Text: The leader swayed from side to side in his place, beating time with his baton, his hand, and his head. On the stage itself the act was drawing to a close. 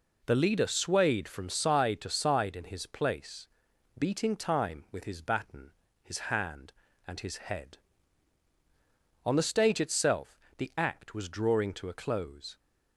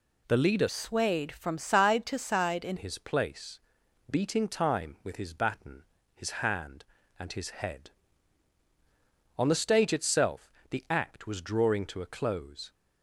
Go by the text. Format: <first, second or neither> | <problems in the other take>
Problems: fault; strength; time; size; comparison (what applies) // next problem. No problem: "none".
first | changes voice from "swayed" to "in"; from 0.6 to 2.7 s; 2.1 s long // pauses between "itself" and "the"; slight; at 10.5 s; 0.20 s long; slight in the first